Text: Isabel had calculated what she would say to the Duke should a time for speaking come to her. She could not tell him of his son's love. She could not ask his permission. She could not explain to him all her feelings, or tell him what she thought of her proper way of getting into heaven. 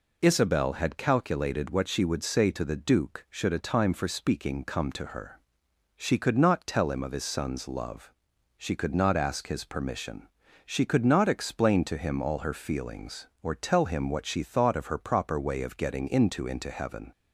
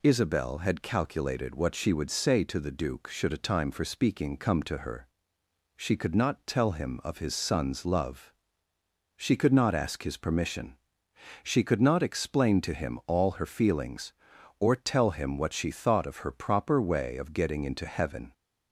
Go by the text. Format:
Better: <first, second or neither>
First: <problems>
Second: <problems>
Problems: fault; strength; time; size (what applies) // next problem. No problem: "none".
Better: second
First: says "into" twice; at 16.4 s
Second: none